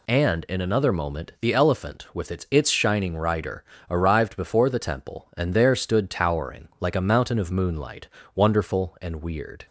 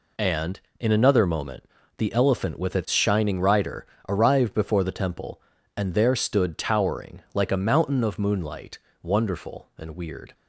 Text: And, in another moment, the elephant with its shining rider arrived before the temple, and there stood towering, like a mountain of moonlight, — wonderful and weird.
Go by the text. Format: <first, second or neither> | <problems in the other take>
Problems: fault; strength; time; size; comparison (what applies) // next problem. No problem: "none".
second | says "its" twice; at 2.4 s // pauses between "rider" and "arrived"; slight; at 3.6 s; 0.24 s long; slight in the second